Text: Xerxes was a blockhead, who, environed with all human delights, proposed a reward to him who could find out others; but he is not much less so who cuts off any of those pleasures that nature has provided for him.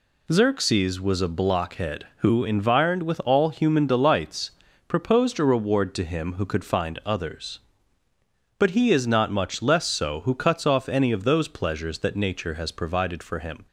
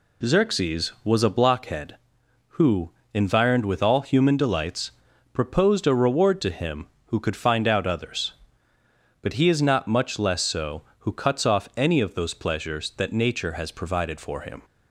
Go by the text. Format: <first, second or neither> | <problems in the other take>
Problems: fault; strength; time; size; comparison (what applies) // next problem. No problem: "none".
second | skips "out"; at 7.0 s